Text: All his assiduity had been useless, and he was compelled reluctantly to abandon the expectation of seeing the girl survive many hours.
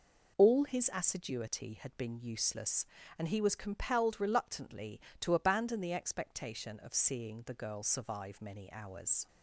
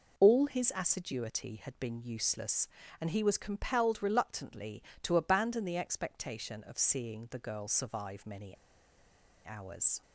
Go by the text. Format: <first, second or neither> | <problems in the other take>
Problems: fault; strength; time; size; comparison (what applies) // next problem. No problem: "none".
first | pauses between "many" and "hours"; noticeable; at 8.5 s; 0.90 s long